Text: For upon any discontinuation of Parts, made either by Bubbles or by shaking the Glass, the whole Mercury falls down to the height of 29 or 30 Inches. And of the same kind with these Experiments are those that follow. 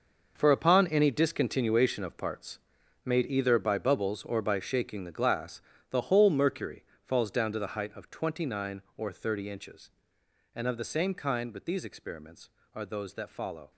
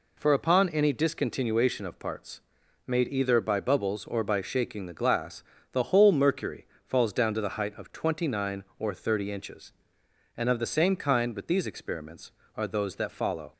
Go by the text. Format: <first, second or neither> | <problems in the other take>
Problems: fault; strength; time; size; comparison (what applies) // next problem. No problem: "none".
second | gets quieter; strong; throughout; 12 dB // pauses between "Mercury" and "falls"; slight; at 6.8 s; 0.18 s long; slight in the second